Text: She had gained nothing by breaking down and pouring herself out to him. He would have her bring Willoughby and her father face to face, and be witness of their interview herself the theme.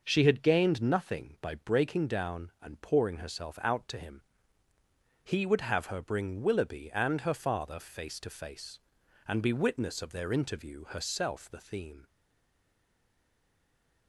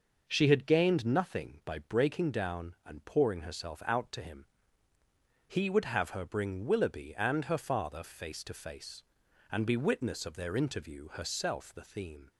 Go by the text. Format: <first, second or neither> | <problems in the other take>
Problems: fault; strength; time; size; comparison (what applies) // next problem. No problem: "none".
second | stays silent after the last word; noticeable; from 12.0 s on; 2.0 s long